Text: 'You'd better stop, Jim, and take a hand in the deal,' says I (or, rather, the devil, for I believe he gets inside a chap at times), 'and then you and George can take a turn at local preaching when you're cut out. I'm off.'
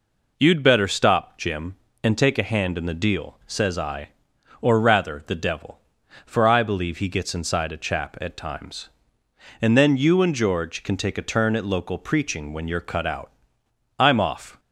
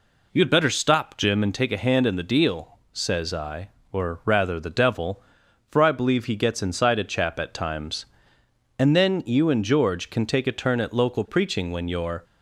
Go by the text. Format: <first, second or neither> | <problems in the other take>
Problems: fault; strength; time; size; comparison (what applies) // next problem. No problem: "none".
first | stops before "cut out I'm off"; at 12.2 s